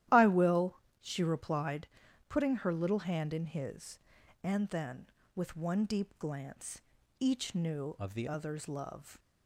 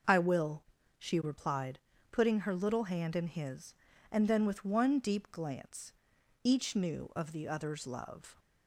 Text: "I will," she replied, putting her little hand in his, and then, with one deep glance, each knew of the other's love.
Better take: second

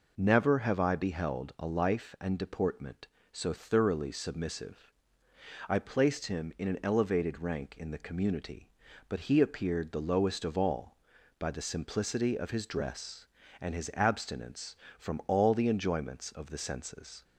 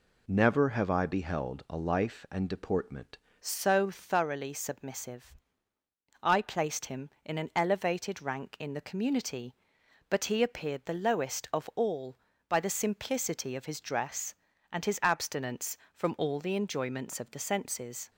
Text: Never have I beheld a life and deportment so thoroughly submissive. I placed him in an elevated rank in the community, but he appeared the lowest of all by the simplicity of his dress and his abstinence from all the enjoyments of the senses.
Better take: first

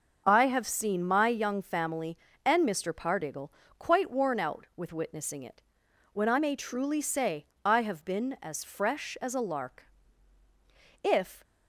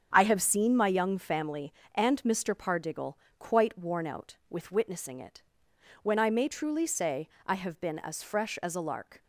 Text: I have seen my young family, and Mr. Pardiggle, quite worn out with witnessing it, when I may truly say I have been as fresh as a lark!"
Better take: second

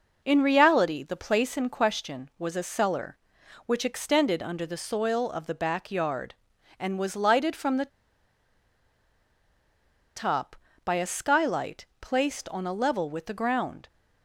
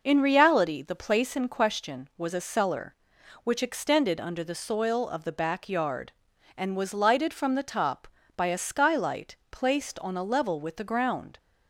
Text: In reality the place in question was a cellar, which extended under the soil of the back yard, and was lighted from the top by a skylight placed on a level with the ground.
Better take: second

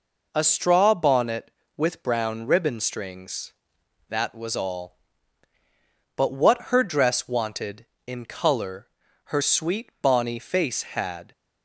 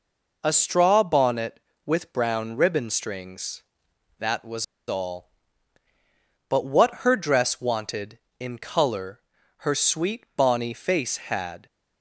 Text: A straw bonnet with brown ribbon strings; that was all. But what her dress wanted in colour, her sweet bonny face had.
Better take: first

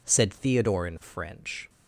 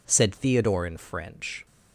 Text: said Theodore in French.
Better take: neither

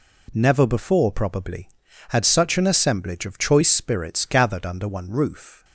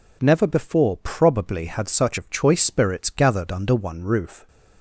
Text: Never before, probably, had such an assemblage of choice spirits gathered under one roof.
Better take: first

